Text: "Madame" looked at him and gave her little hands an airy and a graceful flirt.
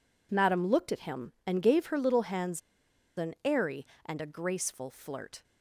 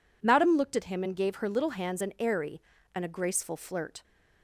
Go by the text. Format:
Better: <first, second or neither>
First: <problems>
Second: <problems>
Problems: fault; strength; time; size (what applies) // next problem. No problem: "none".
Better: second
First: pauses between "hands" and "an"; noticeable; at 2.6 s; 0.56 s long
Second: none